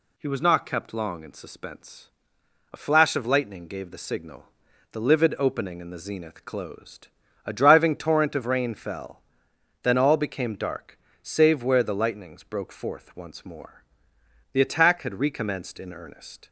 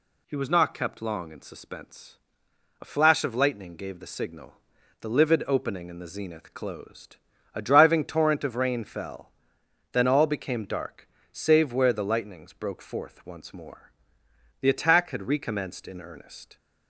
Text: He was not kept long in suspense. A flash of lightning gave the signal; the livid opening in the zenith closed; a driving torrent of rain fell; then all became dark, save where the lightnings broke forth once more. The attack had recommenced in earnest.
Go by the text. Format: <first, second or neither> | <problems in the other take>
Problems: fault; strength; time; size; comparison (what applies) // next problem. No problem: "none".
neither | none